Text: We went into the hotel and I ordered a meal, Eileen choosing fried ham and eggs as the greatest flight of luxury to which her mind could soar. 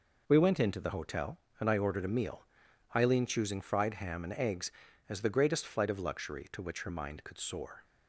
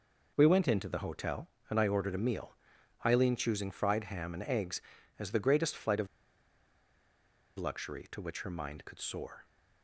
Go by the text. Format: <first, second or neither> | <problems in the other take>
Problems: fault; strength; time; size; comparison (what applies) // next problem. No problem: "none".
first | pauses between "of" and "luxury"; strong; at 6.0 s; 1.5 s long